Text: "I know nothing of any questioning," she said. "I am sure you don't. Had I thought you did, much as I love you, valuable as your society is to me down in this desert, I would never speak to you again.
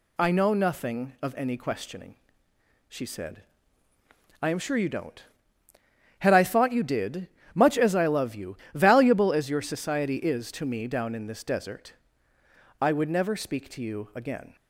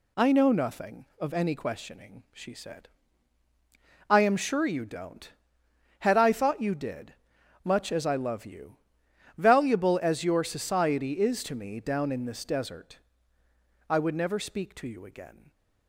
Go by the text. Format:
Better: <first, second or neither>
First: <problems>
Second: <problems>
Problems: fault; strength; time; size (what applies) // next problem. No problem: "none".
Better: neither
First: none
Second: none